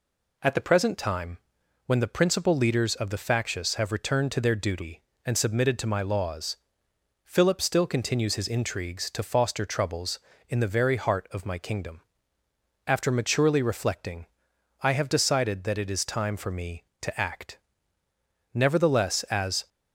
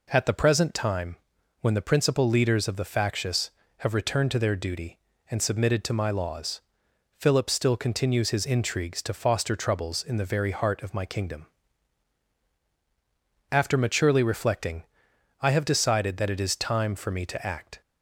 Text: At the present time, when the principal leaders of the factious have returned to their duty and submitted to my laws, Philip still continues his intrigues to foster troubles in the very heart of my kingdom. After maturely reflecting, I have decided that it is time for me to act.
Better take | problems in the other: second | goes on to say "Nevertheless as"; noticeable; from 18.5 s on; 1.1 s long

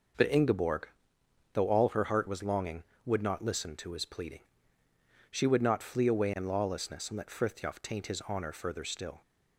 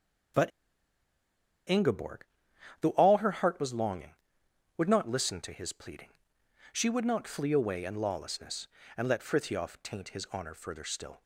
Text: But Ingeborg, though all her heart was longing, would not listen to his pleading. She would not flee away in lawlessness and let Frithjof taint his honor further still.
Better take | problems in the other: first | starts louder than the rest; strong; until 3.1 s; 8.5 dB // pauses between "But" and "Ingeborg"; at 0.5 s; 1.1 s long

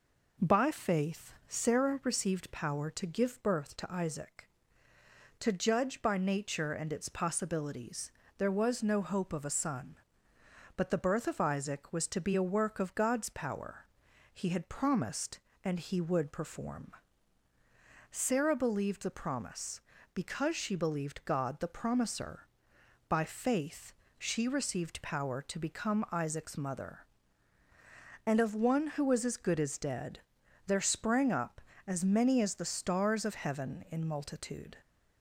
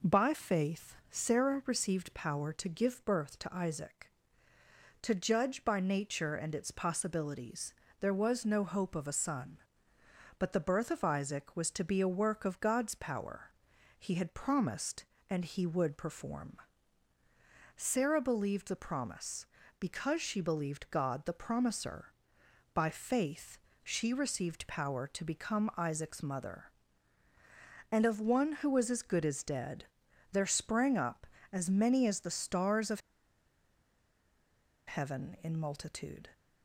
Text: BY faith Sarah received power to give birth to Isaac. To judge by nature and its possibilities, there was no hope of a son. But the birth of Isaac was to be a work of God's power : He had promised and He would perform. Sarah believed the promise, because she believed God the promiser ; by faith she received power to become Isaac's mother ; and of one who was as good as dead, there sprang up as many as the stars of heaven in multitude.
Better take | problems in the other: first | pauses between "faith" and "Sarah"; slight; at 0.9 s; 0.16 s long; slight in the first // pauses between "faith" and "she"; slight; at 23.5 s; 0.24 s long; slight in the first // pauses between "of" and "heaven"; strong; at 33.0 s; 1.8 s long

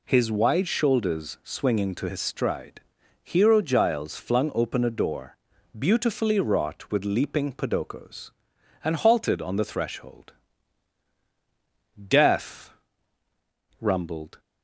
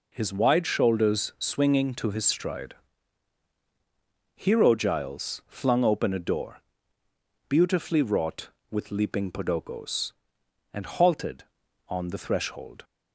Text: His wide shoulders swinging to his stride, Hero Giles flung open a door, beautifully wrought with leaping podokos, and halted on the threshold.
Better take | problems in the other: second | goes on to say "Death rumbled"; strong; from 11.9 s on; 2.4 s long

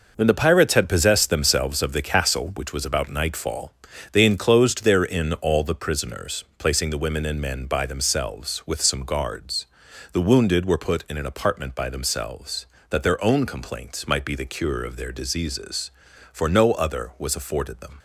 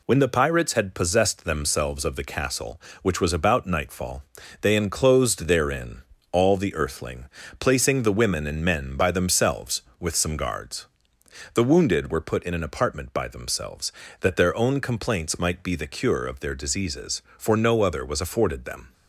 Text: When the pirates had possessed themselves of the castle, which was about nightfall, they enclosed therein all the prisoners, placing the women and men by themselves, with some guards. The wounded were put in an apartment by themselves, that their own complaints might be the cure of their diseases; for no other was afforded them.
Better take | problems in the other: first | pauses between "therein" and "all"; slight; at 6.0 s; 0.30 s long // says "earthling" for "prisoners"; at 6.7 s

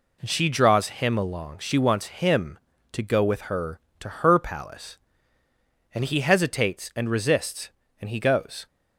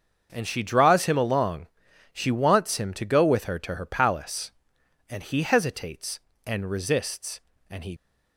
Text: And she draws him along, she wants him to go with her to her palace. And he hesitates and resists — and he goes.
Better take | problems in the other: first | starts louder than the rest; until 1.3 s; 6.5 dB // stops before "goes"; at 7.9 s

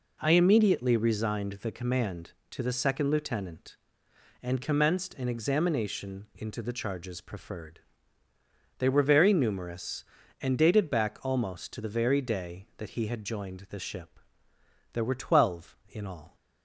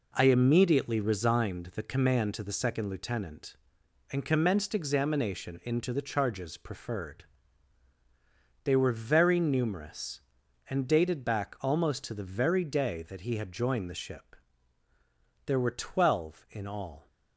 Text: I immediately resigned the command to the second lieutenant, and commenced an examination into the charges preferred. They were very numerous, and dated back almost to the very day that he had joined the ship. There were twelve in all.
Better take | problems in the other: first | skips "an"; at 4.7 s

